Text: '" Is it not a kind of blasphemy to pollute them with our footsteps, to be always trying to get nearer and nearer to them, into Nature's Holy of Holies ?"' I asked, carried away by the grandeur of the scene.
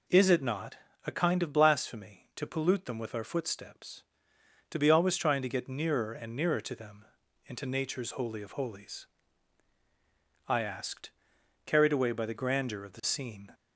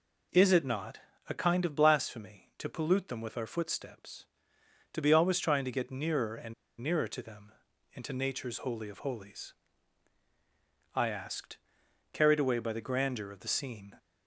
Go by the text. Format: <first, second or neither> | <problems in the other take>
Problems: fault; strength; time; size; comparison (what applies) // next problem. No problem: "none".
first | pauses between "not" and "a"; slight; at 1.0 s; 0.28 s long; slight in the first // pauses between "and" and "nearer"; slight; at 6.5 s; 0.26 s long